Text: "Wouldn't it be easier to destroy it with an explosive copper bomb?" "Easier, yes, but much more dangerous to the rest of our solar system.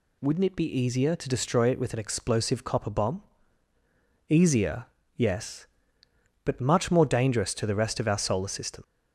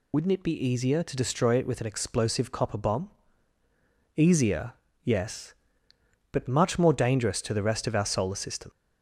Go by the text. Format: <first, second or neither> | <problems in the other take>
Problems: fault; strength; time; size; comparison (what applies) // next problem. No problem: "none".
first | loses the start of "Wouldn't"; at 0.1 s; 60 ms